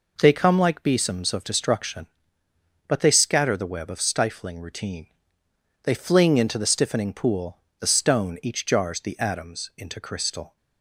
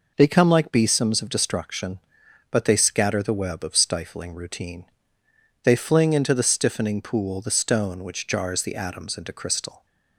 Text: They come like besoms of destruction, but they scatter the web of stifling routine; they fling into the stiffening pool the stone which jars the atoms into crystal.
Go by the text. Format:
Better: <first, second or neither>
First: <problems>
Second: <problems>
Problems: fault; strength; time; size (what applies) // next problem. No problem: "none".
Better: second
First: pauses between "pool" and "the"; slight; at 7.5 s; 0.22 s long // says "each" for "which"; at 8.4 s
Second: none